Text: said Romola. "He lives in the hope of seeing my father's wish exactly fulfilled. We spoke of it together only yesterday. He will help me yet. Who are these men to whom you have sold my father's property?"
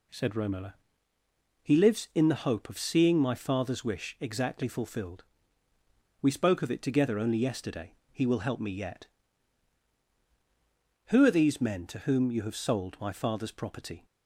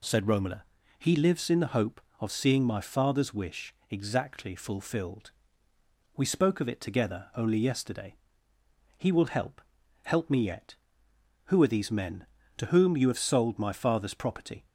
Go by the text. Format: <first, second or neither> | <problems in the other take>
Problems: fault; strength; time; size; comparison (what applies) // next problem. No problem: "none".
first | pauses between "wish" and "exactly"; slight; at 3.7 s; 0.16 s long // says "help" twice; at 10.0 s